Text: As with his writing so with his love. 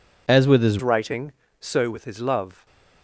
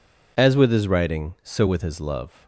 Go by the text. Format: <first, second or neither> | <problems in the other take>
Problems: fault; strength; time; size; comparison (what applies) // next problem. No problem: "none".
second | changes voice at "writing"; from 0.8 s on; 1.8 s long